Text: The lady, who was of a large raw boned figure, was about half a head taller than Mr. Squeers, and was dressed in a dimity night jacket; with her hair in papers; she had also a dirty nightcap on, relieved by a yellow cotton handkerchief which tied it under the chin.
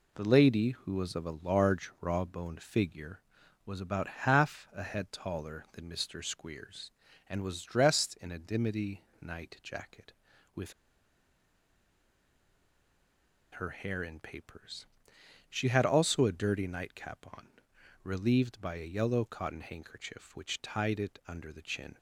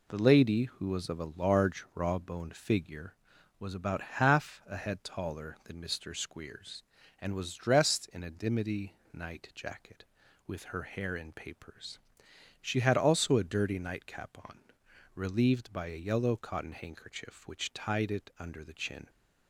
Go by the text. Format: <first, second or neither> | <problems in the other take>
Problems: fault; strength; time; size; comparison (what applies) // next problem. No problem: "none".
second | pauses between "dimity" and "night"; slight; at 9.0 s; 0.18 s long; slight in the second // pauses between "with" and "her"; strong; at 10.7 s; 2.8 s long